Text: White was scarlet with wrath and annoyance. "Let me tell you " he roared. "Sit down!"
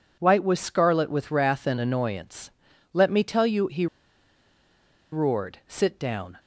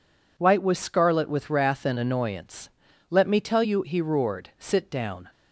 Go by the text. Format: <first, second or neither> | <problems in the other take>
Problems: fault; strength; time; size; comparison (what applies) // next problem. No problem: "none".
second | pauses between "he" and "roared"; strong; at 3.8 s; 1.2 s long